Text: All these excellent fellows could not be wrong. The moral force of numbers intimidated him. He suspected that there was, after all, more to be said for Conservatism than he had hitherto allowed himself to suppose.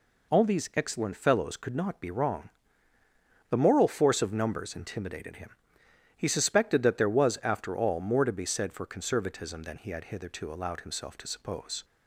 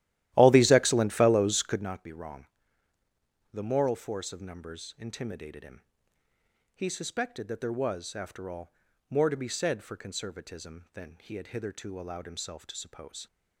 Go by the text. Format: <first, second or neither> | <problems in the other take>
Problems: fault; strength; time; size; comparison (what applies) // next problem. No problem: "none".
first | starts louder than the rest; strong; until 2.0 s; 14 dB